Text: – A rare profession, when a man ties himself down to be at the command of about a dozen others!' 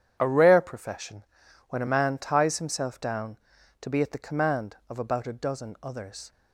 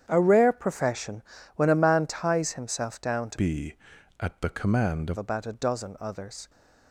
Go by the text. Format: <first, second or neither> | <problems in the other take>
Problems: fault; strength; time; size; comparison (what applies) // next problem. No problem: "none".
first | starts louder than the rest; strong; until 1.1 s; 9 dB; strong in the first // changes voice from "be" to "of"; from 3.3 to 5.1 s; 1.8 s long